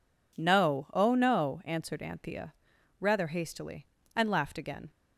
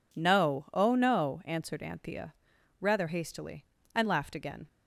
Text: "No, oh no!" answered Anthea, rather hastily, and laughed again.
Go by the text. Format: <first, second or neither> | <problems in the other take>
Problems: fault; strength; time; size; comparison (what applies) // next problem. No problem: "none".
neither | none